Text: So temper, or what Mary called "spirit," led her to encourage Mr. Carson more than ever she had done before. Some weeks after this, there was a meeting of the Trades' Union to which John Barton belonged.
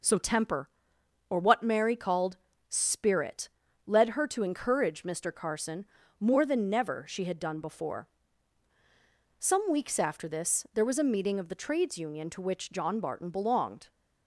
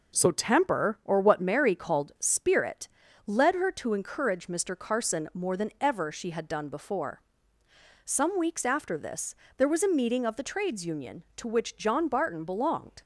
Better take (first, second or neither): second